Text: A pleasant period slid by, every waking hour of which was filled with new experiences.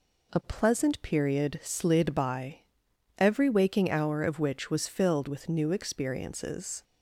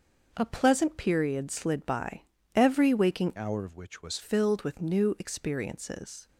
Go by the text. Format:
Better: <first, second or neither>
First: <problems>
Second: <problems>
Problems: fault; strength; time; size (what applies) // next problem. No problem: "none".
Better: first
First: none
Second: starts louder than the rest; until 1.3 s; 6 dB // changes voice from "hour" to "was"; from 3.3 to 4.1 s; 0.8 s long